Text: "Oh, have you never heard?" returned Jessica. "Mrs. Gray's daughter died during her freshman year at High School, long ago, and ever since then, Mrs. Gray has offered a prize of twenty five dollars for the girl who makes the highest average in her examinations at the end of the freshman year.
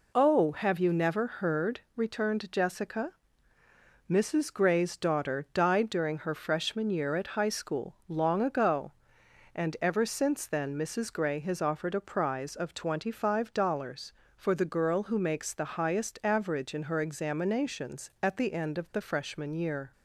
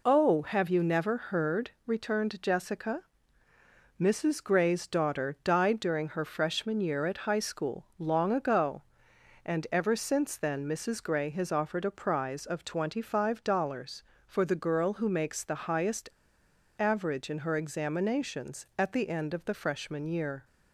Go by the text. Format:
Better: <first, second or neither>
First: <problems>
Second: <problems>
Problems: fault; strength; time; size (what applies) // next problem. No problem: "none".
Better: first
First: none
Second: pauses between "highest" and "average"; noticeable; at 16.0 s; 0.71 s long